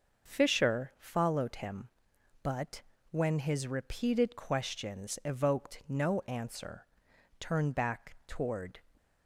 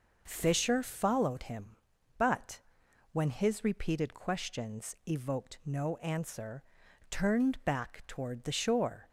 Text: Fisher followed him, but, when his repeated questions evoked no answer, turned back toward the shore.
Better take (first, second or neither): second